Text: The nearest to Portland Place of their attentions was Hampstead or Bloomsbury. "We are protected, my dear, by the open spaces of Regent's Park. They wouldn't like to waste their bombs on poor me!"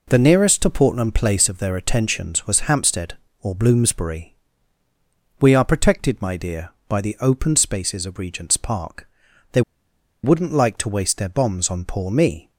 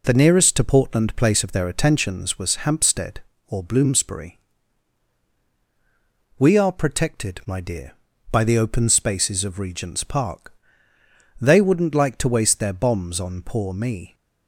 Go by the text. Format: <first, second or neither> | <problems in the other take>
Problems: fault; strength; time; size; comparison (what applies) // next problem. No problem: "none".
second | pauses between "They" and "wouldn't"; noticeable; at 9.6 s; 0.62 s long